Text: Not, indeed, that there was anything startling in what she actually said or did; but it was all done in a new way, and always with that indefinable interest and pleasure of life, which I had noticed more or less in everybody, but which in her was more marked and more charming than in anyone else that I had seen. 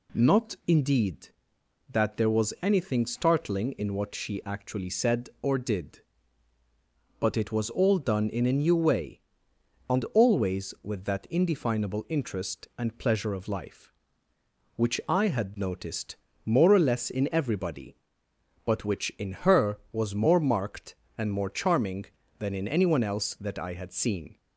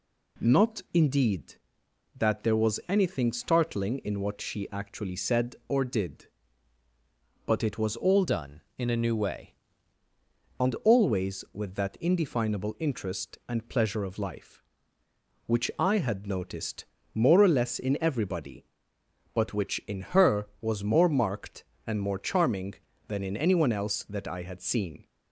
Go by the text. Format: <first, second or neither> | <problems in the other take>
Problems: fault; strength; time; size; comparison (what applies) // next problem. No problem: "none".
first | changes voice from "done" to "way"; from 8.2 to 9.5 s; 1.3 s long // pauses between "noticed" and "more"; slight; at 16.8 s; 0.28 s long; slight in the first